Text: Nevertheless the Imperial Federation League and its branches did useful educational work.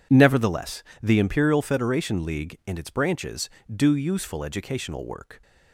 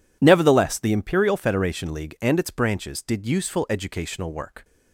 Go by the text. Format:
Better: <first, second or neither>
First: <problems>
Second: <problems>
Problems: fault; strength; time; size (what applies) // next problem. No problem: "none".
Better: second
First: pauses between "Nevertheless" and "the"; slight; at 0.8 s; 0.20 s long // says "do" for "did"; at 3.7 s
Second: none